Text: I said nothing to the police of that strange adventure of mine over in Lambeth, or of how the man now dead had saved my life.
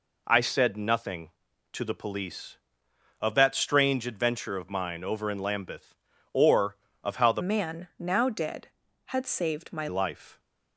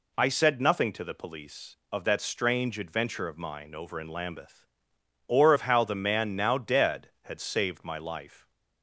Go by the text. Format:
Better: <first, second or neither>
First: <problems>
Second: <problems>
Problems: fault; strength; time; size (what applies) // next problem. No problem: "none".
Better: second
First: changes voice from "man" to "my"; from 7.4 to 9.8 s; 2.4 s long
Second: none